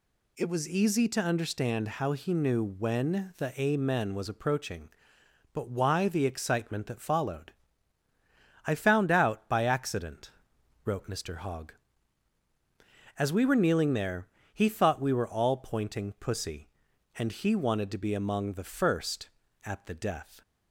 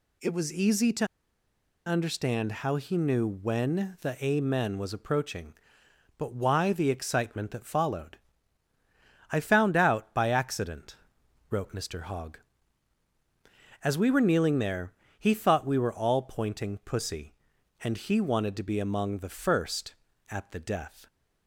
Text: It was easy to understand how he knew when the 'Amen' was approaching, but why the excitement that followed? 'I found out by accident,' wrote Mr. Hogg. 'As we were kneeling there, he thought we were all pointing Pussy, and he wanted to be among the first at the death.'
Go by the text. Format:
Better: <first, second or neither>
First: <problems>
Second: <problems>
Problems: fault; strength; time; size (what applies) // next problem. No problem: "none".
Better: first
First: none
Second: pauses between "to" and "understand"; noticeable; at 1.0 s; 0.80 s long